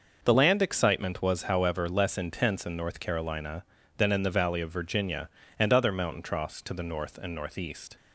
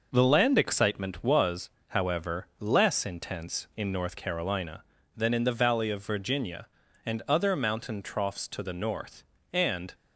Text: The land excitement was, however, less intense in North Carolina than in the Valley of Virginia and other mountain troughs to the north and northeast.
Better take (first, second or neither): first